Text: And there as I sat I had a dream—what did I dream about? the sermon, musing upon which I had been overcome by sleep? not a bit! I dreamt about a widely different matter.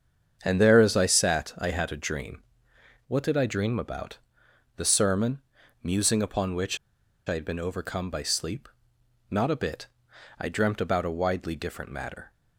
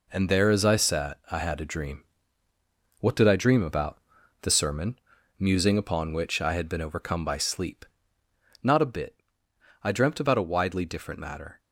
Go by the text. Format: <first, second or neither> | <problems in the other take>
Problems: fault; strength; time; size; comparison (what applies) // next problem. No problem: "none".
second | starts louder than the rest; strong; until 1.4 s; 7.5 dB // pauses between "which" and "I"; noticeable; at 6.7 s; 0.50 s long